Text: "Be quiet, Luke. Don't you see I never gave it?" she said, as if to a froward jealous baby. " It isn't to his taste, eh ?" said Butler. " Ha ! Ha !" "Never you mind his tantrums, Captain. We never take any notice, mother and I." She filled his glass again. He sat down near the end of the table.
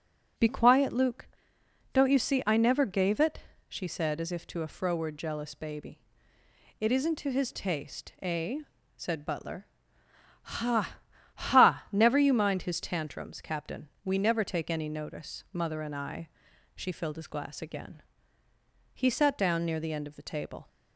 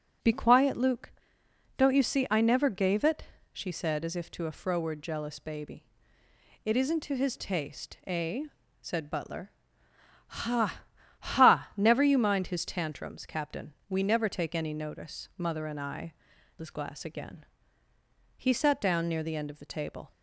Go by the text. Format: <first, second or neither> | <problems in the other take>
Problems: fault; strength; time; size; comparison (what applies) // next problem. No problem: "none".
first | starts louder than the rest; strong; until 1.8 s; 10.5 dB; strong in the first // skips "She filled"; at 16.3 s